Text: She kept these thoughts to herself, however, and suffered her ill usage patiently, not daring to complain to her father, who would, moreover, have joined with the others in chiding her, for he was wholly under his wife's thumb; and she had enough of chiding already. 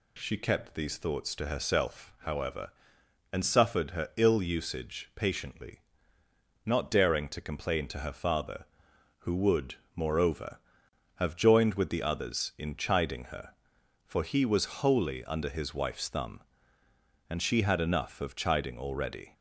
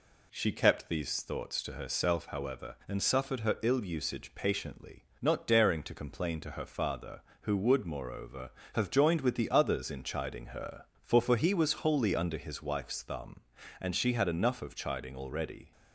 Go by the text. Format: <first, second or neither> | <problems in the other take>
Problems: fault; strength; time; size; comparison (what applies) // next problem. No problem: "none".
first | says "for" twice; at 11.1 s